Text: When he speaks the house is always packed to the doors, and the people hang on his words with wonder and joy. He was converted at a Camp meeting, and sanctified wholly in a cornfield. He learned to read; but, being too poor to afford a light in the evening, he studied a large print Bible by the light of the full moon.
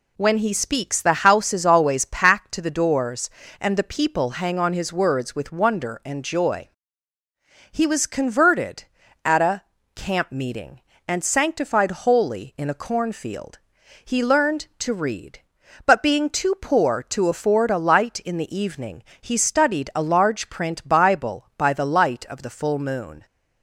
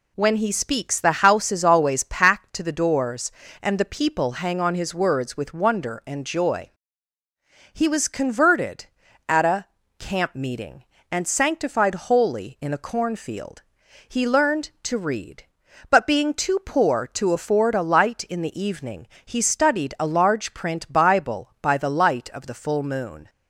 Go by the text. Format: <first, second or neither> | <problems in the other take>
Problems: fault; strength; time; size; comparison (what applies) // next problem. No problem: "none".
neither | pauses between "a" and "Camp"; slight; the same in both